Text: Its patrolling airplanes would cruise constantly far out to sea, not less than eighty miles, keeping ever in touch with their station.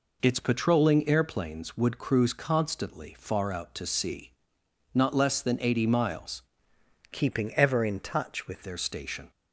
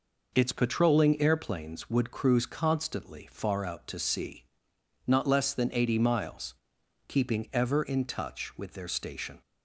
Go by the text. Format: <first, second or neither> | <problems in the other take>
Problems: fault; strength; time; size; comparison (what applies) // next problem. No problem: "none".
second | changes voice from "keeping" to "with"; from 7.1 to 8.6 s; 1.5 s long